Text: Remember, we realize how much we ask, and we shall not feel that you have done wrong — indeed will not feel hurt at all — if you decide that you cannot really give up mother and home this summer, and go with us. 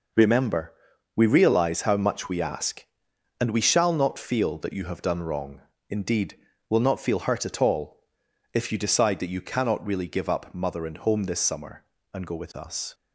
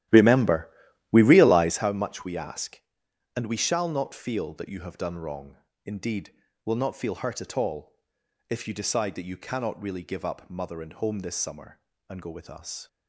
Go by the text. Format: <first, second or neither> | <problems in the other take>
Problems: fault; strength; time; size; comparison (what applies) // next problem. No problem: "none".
first | starts louder than the rest; strong; until 1.9 s; 13.5 dB